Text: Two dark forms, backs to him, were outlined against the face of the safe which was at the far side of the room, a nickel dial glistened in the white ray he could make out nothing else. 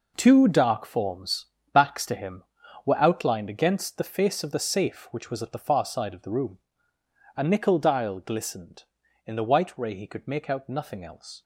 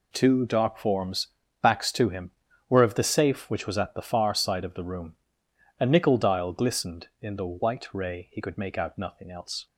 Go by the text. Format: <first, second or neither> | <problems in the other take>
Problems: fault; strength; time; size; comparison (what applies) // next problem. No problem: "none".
first | skips "outlined against the face"; at 2.8 s